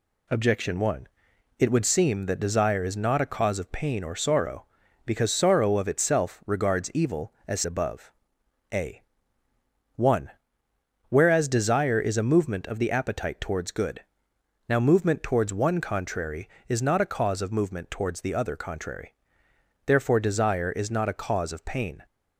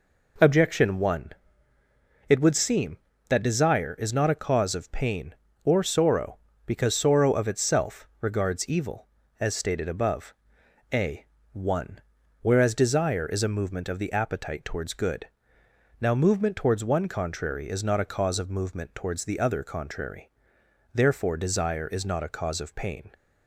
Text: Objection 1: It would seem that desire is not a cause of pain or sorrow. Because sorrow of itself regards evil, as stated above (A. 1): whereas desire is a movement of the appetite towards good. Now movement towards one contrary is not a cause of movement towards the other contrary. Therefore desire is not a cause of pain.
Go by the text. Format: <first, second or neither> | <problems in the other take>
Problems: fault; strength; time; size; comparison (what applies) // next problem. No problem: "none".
second | skips "stated"; at 7.6 s